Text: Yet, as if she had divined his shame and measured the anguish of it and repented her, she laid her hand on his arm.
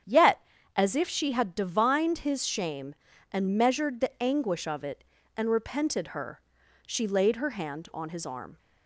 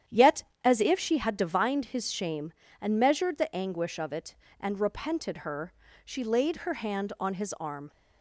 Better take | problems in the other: neither | starts louder than the rest; strong; the same in both

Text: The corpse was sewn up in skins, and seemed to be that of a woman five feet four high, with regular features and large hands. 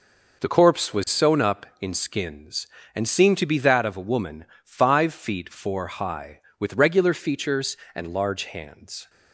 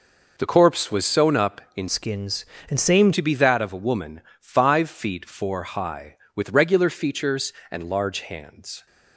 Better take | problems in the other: first | changes voice from "skins" to "seemed"; from 1.8 to 3.1 s; 1.3 s long // pauses between "woman" and "five"; slight; at 4.2 s; 0.18 s long; slight in the first

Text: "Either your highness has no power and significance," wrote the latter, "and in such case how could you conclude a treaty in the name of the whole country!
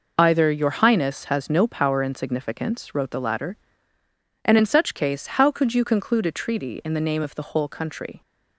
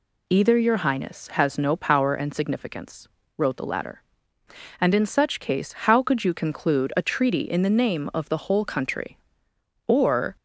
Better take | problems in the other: first | pauses between "case" and "how"; slight; at 5.7 s; 0.16 s long // goes on to say "or"; from 9.8 s on; 0.50 s long

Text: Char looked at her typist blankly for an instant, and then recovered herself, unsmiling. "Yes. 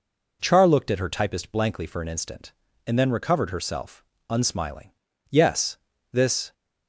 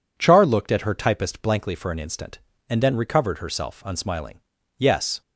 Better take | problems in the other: second | goes on to say "This"; slight; from 6.1 s on; 0.40 s long

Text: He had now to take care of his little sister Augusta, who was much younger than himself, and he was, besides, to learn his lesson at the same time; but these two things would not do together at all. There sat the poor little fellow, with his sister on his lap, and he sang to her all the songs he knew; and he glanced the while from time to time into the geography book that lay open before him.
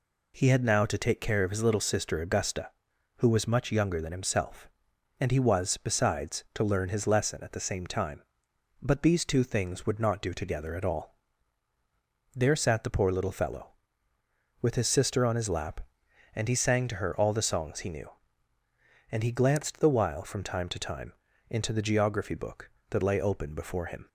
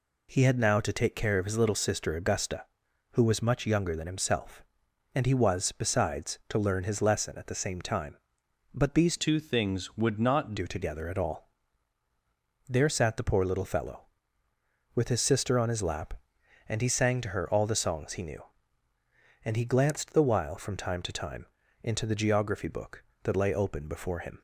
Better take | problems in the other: first | changes voice from "two" to "not"; from 9.1 to 10.5 s; 1.4 s long // pauses between "time" and "into"; slight; at 21.4 s; 0.36 s long; slight in the first

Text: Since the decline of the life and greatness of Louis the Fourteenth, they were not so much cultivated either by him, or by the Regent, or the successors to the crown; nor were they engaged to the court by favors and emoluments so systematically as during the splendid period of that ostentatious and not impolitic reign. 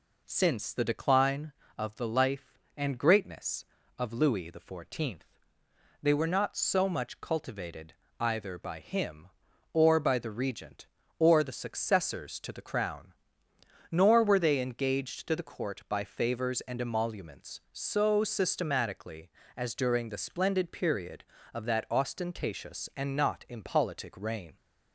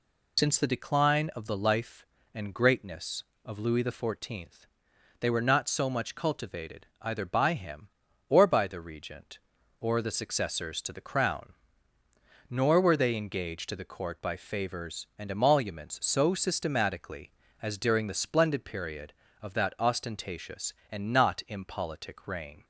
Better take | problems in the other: first | loses the start of "Since"; at 0.3 s; 60 ms // pauses between "cultivated" and "either"; slight; at 6.8 s; 0.16 s long; slight in the first

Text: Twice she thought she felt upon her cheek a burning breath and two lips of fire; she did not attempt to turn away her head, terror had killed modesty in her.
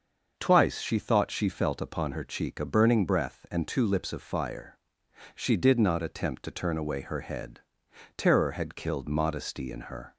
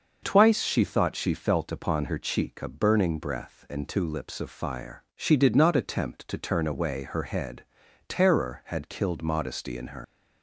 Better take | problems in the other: first | starts louder than the rest; noticeable; until 1.2 s; 6 dB; also in the first // leaves "her" unfinished; at 10.0 s; 90 ms

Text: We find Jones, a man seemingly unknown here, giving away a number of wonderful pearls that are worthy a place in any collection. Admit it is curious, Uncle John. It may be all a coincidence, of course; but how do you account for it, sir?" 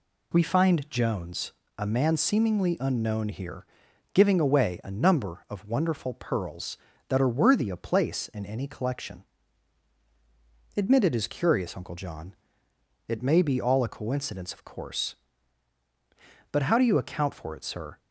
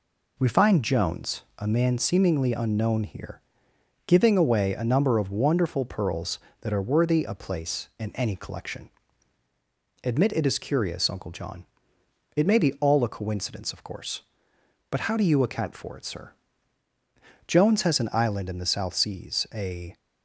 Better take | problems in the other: first | goes on to say "Jones has an island in the South Seas a"; strong; from 17.4 s on; 2.5 s long

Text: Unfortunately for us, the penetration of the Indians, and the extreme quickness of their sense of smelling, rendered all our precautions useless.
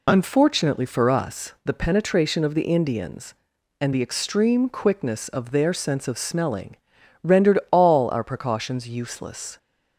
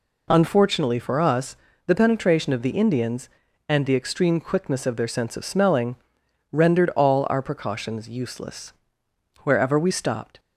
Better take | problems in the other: first | goes on to say "Wherever we stopped"; noticeable; from 9.4 s on; 0.96 s long

